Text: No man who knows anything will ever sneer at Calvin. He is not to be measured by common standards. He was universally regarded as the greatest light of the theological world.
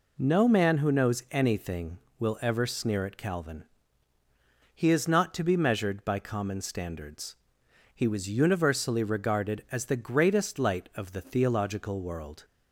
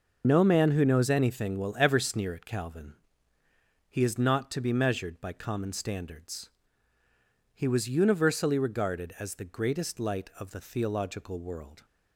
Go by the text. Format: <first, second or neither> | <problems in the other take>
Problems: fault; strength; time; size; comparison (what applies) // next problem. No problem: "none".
first | loses the start of "No"; at 0.2 s; 45 ms